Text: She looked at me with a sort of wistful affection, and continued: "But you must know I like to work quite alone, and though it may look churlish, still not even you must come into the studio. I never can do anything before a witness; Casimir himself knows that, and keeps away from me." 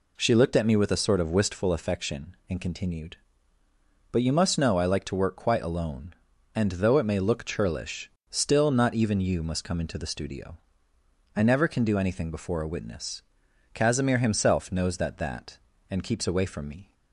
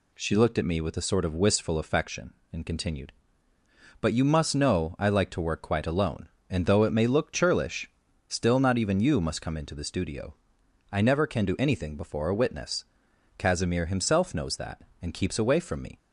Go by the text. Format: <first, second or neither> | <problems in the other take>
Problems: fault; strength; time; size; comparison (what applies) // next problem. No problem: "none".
second | says "that" twice; at 15.1 s